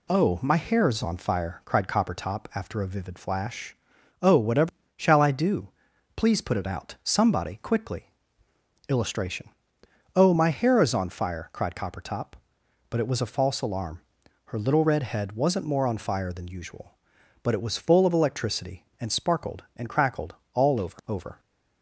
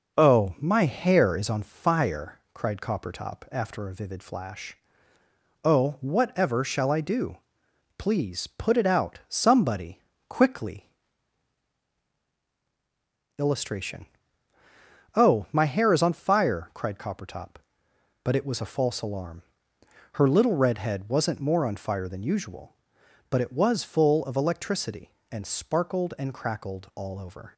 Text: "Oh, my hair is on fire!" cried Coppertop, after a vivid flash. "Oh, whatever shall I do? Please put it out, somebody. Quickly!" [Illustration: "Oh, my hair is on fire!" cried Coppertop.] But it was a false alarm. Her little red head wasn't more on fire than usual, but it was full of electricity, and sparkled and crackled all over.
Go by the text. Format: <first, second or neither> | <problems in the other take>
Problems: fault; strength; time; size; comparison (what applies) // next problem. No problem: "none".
second | pauses between "whatever" and "shall"; slight; at 4.6 s; 0.26 s long // pauses between "crackled" and "all"; slight; at 20.3 s; 0.18 s long // says "over" twice; at 21.0 s